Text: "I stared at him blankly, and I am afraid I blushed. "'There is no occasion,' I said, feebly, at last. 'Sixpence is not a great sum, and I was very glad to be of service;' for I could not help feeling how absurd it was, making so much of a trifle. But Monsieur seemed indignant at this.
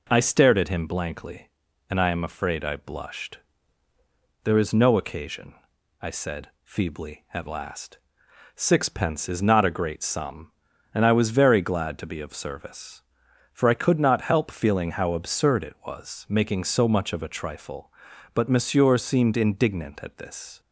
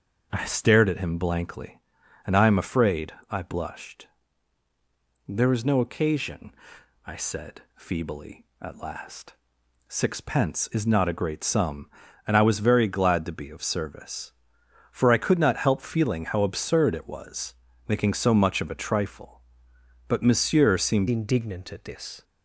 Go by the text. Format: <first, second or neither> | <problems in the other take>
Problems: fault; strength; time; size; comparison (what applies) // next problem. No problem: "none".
first | starts louder than the rest; until 1.3 s; 6.5 dB // pauses between "afraid" and "I"; slight; at 3.1 s; 0.16 s long // changes voice at "indignant"; from 21.0 s on; 1.2 s long